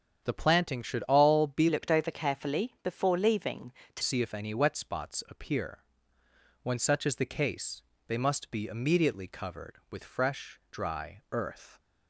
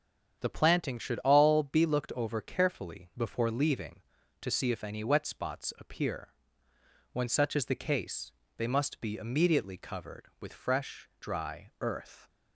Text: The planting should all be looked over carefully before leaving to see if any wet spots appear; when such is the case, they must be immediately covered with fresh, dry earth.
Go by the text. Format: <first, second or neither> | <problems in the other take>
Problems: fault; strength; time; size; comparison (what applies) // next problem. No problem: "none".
second | starts louder than the rest; strong; until 1.2 s; 8 dB; strong in the second // changes voice from "looked" to "to"; from 1.6 to 4.0 s; 2.4 s long